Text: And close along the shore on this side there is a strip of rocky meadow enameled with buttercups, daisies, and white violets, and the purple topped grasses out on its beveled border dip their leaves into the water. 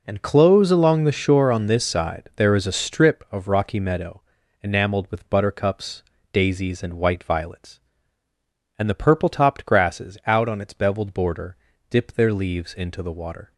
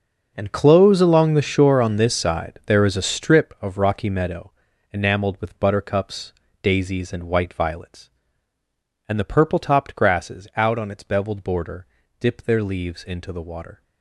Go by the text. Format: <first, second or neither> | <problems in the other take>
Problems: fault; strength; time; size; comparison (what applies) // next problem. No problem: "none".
first | gets quieter; strong; throughout; 14 dB // pauses between "meadow" and "enameled"; at 4.5 s; 0.40 s long; also in the first // pauses between "border" and "dip"; slight; at 11.8 s; 0.34 s long; slight in the first